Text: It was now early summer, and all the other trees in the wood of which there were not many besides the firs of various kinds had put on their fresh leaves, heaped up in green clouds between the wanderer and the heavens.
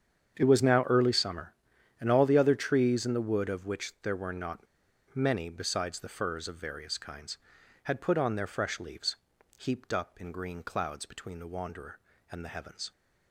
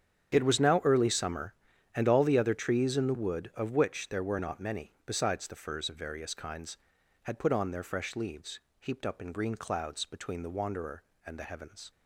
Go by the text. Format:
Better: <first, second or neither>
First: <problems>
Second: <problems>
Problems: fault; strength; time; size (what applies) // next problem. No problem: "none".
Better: second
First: starts louder than the rest; strong; until 1.3 s; 8 dB // pauses between "not" and "many"; noticeable; at 4.6 s; 0.51 s long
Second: starts louder than the rest; strong; until 1.3 s; 9 dB